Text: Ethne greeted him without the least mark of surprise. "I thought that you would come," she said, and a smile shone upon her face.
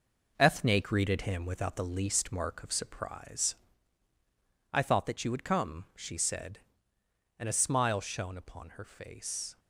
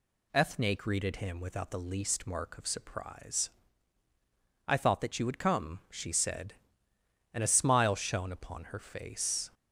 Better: second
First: gets quieter; noticeable; throughout; 5.5 dB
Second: none

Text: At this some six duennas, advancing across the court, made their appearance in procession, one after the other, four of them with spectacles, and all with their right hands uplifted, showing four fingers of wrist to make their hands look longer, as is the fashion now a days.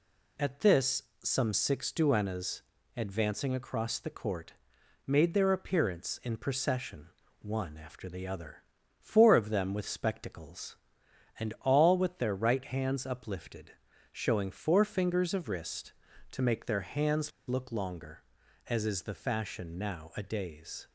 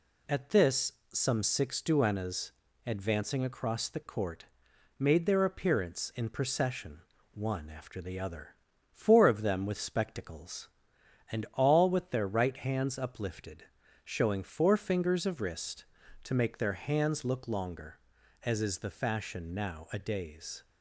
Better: second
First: pauses between "this" and "some"; slight; at 1.0 s; 0.20 s long // pauses between "hands" and "look"; slight; at 17.3 s; 0.16 s long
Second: pauses between "this" and "some"; slight; at 0.9 s; 0.20 s long

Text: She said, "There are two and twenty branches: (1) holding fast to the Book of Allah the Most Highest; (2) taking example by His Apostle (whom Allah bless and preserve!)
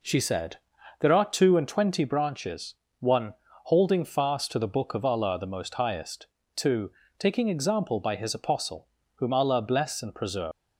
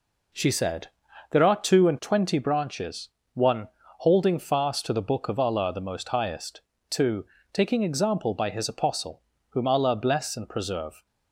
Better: second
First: leaves "preserve" unfinished; at 10.5 s; 195 ms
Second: none

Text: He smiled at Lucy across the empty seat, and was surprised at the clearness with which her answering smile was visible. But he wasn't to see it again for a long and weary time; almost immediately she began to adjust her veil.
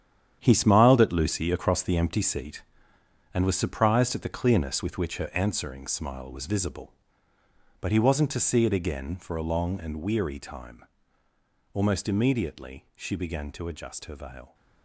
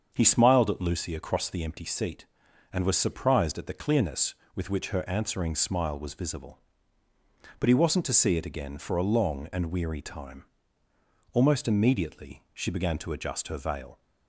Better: second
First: gets quieter; strong; throughout; 10.5 dB // starts louder than the rest; strong; until 1.4 s; 9.5 dB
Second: starts louder than the rest; until 1.1 s; 7 dB

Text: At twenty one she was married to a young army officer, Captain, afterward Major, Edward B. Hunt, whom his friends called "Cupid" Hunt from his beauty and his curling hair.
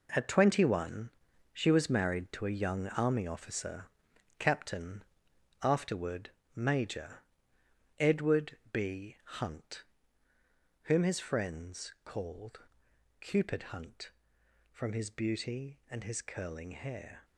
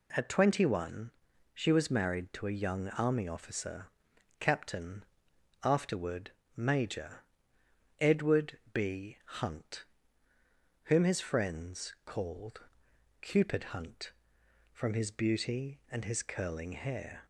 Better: second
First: gets quieter; strong; throughout; 9 dB // pauses between "one" and "she"; at 1.1 s; 0.42 s long // pauses between "afterward" and "Major"; slight; at 6.3 s; 0.26 s long // pauses between "Edward" and "B"; slight; at 8.5 s; 0.16 s long // pauses between "called" and "Cupid"; noticeable; at 12.5 s; 0.62 s long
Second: pauses between "one" and "she"; at 1.1 s; 0.42 s long // pauses between "afterward" and "Major"; slight; at 6.3 s; 0.26 s long // pauses between "Edward" and "B"; slight; at 8.5 s; 0.16 s long // pauses between "called" and "Cupid"; noticeable; at 12.5 s; 0.62 s long

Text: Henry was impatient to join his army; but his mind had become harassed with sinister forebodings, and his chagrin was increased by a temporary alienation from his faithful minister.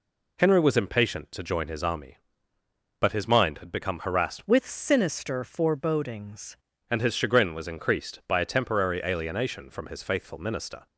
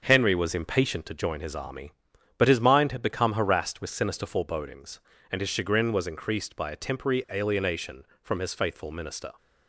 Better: second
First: changes voice from "with" to "forebodings"; from 4.4 to 6.5 s; 2.1 s long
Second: none

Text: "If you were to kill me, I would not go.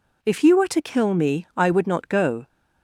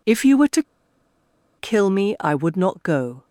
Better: first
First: none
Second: pauses between "to" and "kill"; noticeable; at 0.6 s; 0.95 s long

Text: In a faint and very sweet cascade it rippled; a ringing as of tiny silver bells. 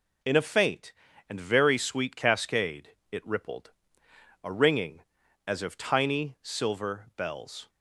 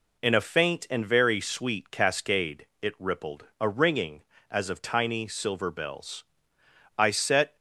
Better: first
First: pauses between "cascade" and "it"; slight; at 2.9 s; 0.20 s long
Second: pauses between "cascade" and "it"; slight; at 2.6 s; 0.16 s long // goes on to say "I set"; from 6.9 s on; 0.58 s long

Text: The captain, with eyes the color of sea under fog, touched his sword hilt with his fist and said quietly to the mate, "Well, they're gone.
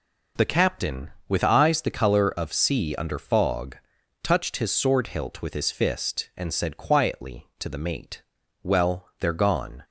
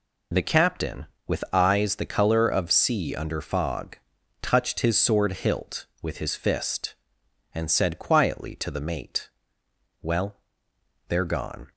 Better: first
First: none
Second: loses the start of "The"; at 0.3 s; 20 ms

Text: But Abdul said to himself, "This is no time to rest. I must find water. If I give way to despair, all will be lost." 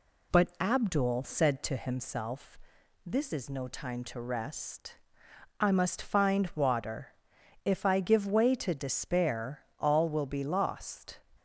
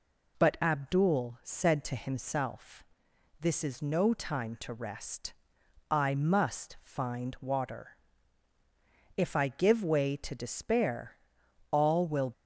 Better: first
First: none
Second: stops before "be lost"; at 12.3 s

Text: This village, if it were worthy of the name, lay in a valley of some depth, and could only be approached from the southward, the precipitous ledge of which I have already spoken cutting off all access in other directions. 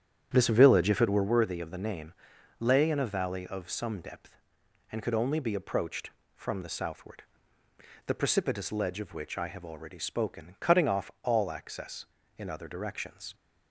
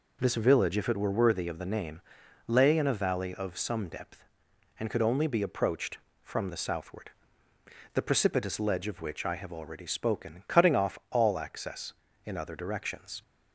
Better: second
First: starts louder than the rest; strong; until 1.3 s; 9 dB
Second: none

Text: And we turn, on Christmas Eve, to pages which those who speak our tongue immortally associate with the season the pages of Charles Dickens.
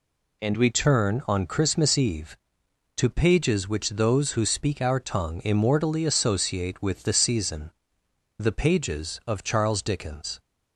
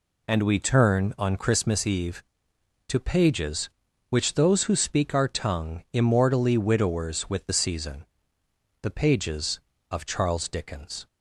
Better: first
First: pauses between "season" and "the"; noticeable; at 7.7 s; 0.68 s long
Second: says "widowers" for "associate"; at 6.5 s // pauses between "season" and "the"; noticeable; at 8.0 s; 0.78 s long

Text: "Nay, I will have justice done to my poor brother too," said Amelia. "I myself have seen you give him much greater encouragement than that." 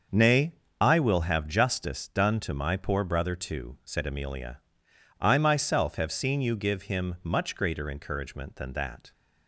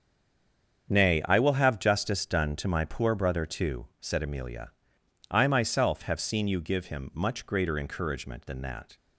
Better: first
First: starts louder than the rest; until 1.3 s; 6.5 dB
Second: stays silent before the first word; slight; until 0.8 s; 0.8 s long // starts louder than the rest; strong; until 1.9 s; 7.5 dB

